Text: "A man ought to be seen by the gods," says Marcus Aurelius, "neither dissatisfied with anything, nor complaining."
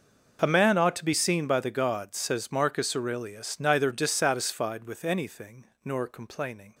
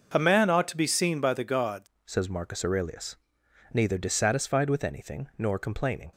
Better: first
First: none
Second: changes voice at "says"; from 2.0 s on; 4.1 s long

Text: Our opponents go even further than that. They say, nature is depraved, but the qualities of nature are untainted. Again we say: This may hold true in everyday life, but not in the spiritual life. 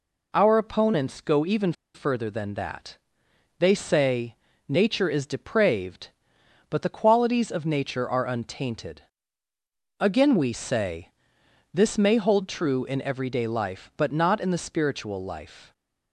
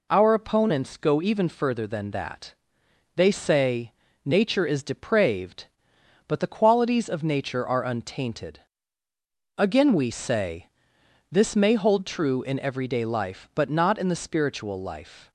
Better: second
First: pauses between "even" and "further"; slight; at 1.7 s; 0.22 s long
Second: none

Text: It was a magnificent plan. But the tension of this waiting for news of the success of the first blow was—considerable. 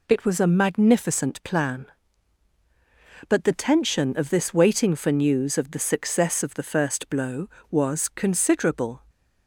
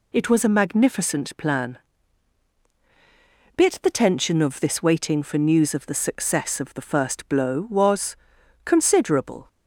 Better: first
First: none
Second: says "Bit" for "But"; at 3.5 s

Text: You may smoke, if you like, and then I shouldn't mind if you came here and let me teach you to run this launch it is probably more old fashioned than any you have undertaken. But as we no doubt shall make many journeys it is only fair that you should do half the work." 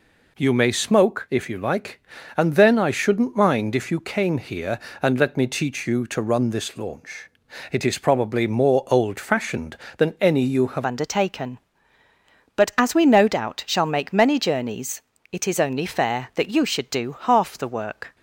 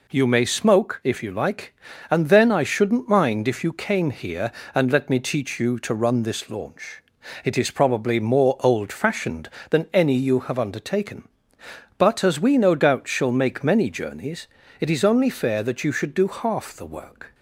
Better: second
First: pauses between "launch" and "it"; at 7.2 s; 0.40 s long // changes voice at "undertaken"; from 10.8 s on; 7.3 s long // pauses between "journeys" and "it"; slight; at 15.0 s; 0.32 s long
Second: pauses between "launch" and "it"; at 7.0 s; 0.40 s long // pauses between "journeys" and "it"; slight; at 14.4 s; 0.32 s long

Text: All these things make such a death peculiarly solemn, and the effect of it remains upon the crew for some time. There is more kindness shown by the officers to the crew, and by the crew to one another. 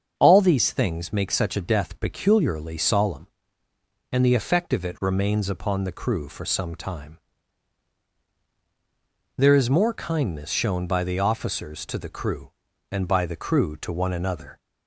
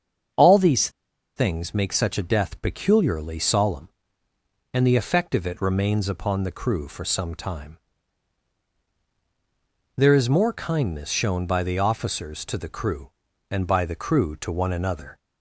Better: first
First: starts louder than the rest; strong; until 1.1 s; 7 dB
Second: starts louder than the rest; strong; until 1.8 s; 7 dB // pauses between "these" and "things"; noticeable; at 0.8 s; 0.47 s long

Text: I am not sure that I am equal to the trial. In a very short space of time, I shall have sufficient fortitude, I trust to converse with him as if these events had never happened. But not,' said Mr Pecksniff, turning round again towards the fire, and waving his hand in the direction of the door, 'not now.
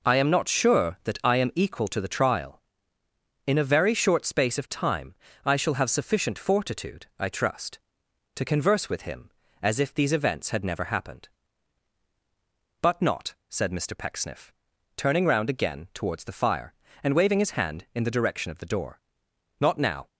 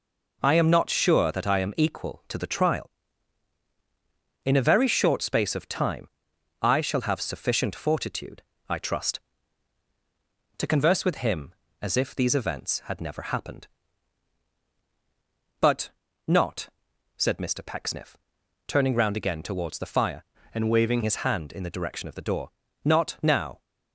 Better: first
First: none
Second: pauses between "But" and "not"; slight; at 15.9 s; 0.36 s long // changes voice from "and" to "waving"; from 20.5 to 21.0 s; 0.5 s long

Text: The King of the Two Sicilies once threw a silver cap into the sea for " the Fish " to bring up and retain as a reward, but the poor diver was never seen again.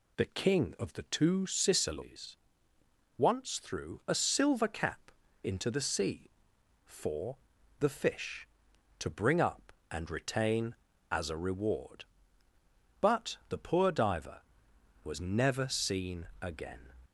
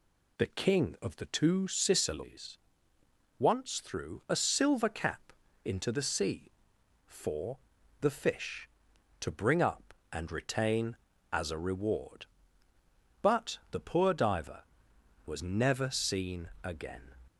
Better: neither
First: pauses between "Sicilies" and "once"; noticeable; at 2.3 s; 0.80 s long // pauses between "cap" and "into"; slight; at 5.1 s; 0.32 s long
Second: pauses between "Sicilies" and "once"; noticeable; at 2.5 s; 0.80 s long // pauses between "cap" and "into"; slight; at 5.3 s; 0.32 s long

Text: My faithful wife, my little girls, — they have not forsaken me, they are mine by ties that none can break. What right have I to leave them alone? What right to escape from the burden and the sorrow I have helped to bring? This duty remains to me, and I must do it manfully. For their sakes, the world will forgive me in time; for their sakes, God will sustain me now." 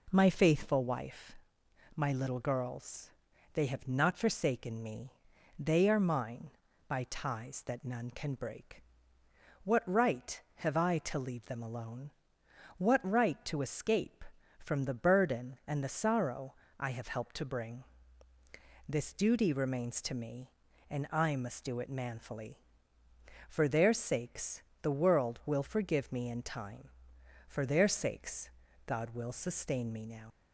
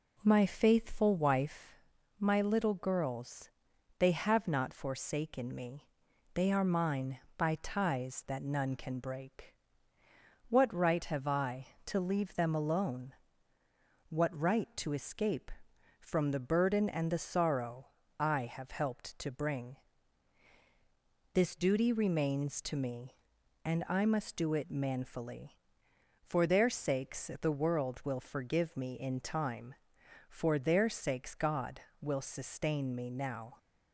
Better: second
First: pauses between "sorrow" and "I"; slight; at 16.5 s; 0.24 s long // leaves "now" unfinished; at 30.3 s; 85 ms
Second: pauses between "sorrow" and "I"; slight; at 17.8 s; 0.32 s long

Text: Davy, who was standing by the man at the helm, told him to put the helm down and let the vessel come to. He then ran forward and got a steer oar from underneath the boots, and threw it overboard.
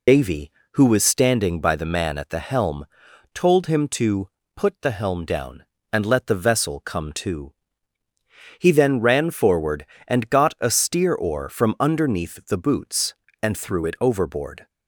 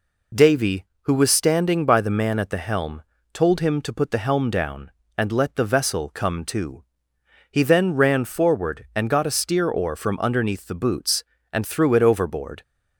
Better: second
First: loses the start of "Davy"; at 0.0 s; 70 ms // pauses between "to" and "put"; slight; at 4.2 s; 0.28 s long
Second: none

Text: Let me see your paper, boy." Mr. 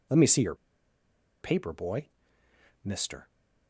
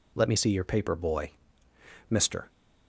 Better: second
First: pauses between "your" and "paper"; noticeable; at 0.5 s; 0.87 s long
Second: none

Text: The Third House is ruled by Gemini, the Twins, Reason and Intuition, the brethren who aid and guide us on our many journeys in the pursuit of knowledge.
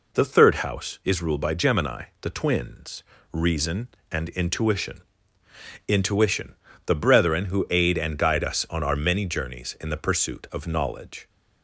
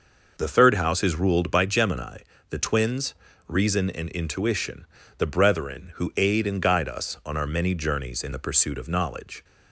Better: second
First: says "Intuition" twice; at 5.8 s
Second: none

